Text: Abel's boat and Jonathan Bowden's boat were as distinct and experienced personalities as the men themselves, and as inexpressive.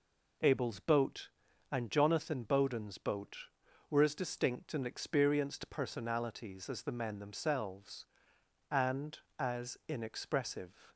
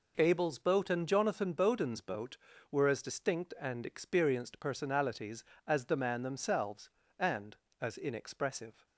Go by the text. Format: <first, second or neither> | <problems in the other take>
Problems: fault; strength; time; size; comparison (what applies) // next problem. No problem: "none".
first | says "man" for "men"; at 5.9 s